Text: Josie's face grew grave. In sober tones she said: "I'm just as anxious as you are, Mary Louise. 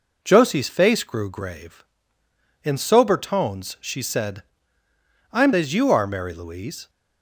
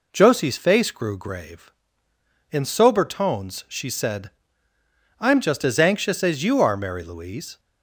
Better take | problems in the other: second | skips "just as anxious"; at 5.5 s

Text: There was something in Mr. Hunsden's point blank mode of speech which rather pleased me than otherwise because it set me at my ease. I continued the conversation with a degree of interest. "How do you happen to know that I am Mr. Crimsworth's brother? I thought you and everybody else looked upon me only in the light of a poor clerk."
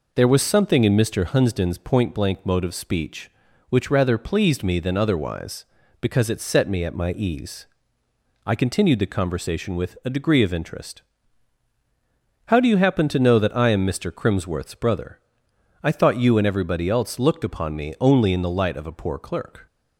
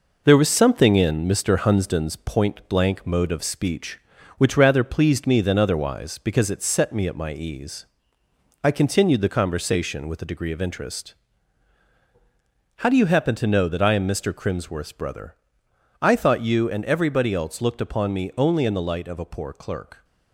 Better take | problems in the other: first | gets quieter; noticeable; throughout; 4.5 dB

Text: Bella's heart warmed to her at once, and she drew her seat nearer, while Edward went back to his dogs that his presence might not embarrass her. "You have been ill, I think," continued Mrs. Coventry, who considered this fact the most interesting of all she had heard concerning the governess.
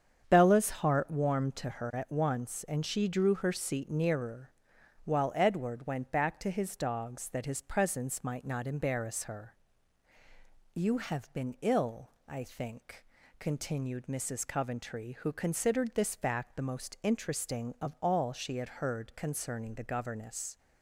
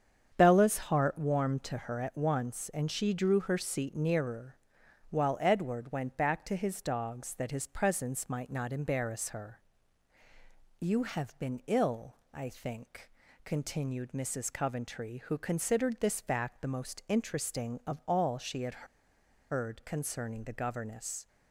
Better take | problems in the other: first | starts louder than the rest; strong; until 1.4 s; 7.5 dB; strong in the first // pauses between "had" and "heard"; noticeable; at 18.8 s; 0.66 s long

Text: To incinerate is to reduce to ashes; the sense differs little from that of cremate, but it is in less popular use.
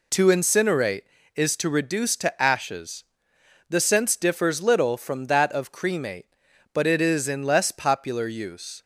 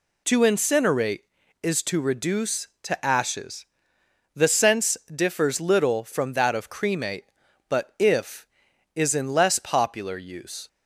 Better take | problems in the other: first | pauses between "sense" and "differs"; slight; at 4.9 s; 0.16 s long // says "if" for "it"; at 7.9 s

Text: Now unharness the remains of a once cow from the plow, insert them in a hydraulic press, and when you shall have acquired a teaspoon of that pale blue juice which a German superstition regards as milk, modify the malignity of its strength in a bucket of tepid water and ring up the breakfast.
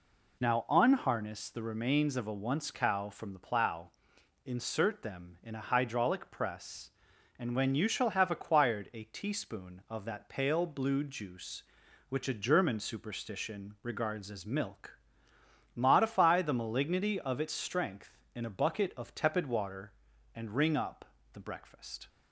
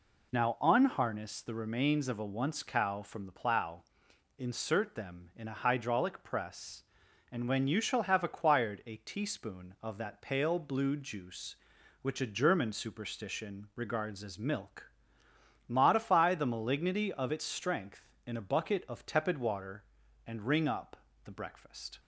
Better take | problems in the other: neither | pauses between "up" and "the"; slight; the same in both

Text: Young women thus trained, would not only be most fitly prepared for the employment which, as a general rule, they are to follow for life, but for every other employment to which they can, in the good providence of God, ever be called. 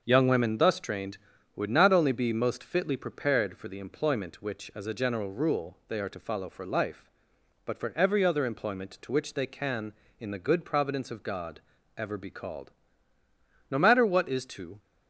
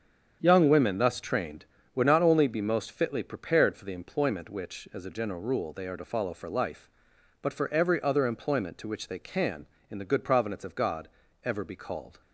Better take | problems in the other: second | starts louder than the rest; until 1.0 s; 6.5 dB; strong in the second // goes on to say "No matter what is to"; noticeable; from 13.6 s on; 1.1 s long

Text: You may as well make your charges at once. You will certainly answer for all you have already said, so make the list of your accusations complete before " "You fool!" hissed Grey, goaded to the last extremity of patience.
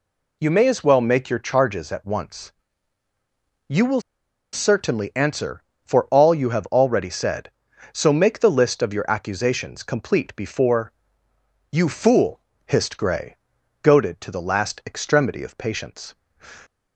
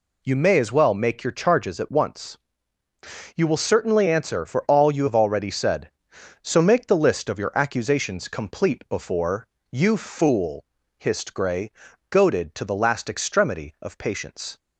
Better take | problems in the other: second | pauses between "will" and "certainly"; noticeable; at 4.0 s; 0.52 s long

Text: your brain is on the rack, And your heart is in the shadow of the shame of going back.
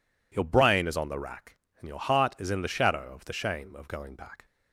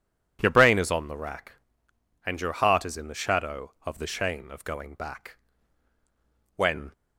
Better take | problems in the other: first | goes on to say "When"; slight; from 6.5 s on; 0.36 s long

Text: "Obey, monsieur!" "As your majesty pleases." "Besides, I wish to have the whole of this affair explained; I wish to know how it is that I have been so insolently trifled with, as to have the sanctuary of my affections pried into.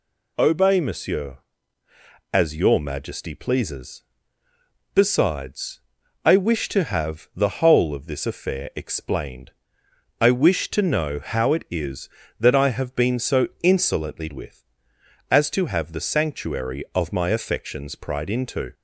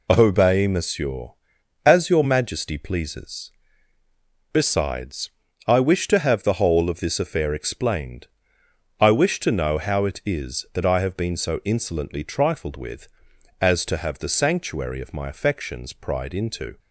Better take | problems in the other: second | skips "trifled"; at 14.3 s

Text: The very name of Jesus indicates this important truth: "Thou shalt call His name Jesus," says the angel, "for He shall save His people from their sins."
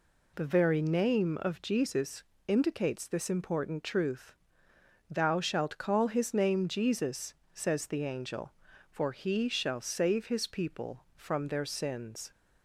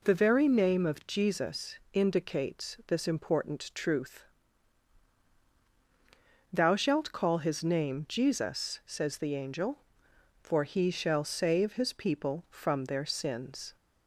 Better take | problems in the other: neither | pauses between "Jesus" and "indicates"; slight; the same in both

